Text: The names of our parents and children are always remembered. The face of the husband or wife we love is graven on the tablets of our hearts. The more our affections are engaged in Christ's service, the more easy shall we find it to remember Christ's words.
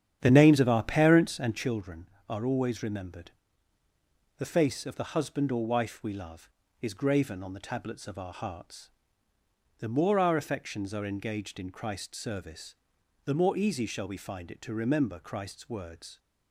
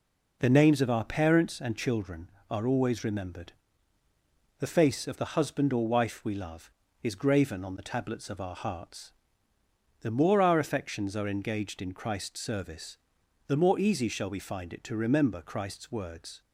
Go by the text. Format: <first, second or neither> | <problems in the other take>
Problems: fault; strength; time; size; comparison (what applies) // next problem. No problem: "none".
second | starts louder than the rest; strong; until 1.7 s; 9.5 dB